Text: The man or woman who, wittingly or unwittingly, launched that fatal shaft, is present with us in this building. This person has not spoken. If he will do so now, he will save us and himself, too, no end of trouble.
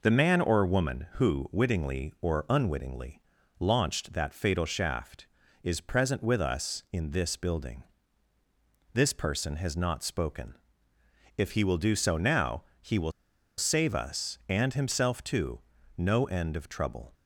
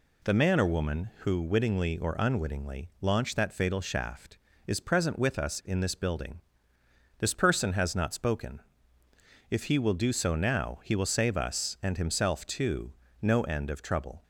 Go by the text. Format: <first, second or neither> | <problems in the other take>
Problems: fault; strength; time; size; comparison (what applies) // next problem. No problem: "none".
second | pauses between "will" and "save"; noticeable; at 13.1 s; 0.46 s long